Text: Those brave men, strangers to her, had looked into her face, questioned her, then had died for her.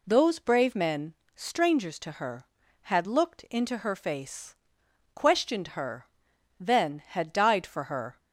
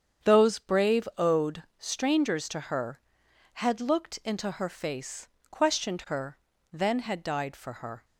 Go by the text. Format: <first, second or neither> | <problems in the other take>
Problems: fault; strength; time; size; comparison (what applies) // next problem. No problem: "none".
first | starts louder than the rest; strong; until 1.3 s; 8 dB // says "owed" for "men"; at 1.1 s